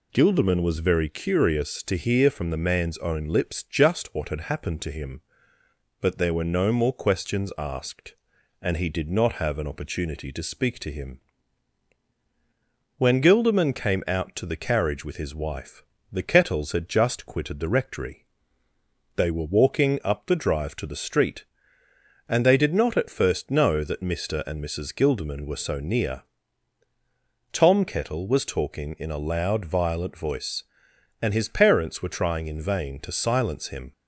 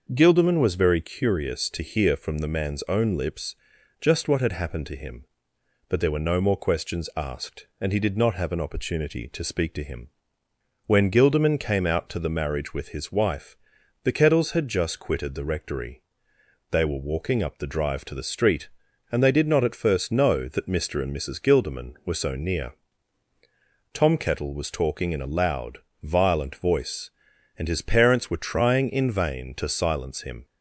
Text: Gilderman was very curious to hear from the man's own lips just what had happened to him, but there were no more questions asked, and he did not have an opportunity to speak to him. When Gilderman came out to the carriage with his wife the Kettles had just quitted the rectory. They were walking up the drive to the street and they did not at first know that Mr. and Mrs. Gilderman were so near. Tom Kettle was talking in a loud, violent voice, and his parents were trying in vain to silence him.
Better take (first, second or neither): first